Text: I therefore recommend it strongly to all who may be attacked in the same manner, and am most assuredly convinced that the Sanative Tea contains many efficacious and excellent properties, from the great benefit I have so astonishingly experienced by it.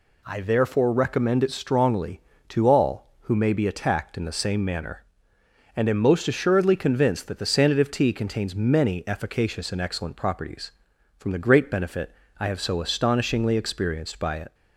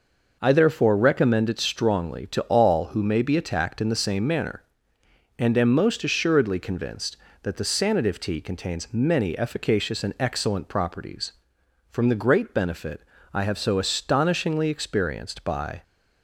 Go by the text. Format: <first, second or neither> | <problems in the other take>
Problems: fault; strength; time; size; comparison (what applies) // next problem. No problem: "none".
first | pauses between "benefit" and "I"; slight; at 13.0 s; 0.32 s long; slight in the first // stops before "it"; at 15.8 s